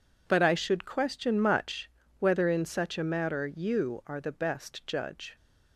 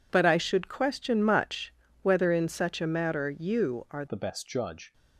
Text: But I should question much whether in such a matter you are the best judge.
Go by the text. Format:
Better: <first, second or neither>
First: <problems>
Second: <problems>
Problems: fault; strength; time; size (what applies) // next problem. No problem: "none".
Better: first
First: pauses between "much" and "whether"; slight; at 1.9 s; 0.30 s long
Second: pauses between "much" and "whether"; slight; at 1.7 s; 0.30 s long // changes voice at "the"; from 4.0 s on; 0.9 s long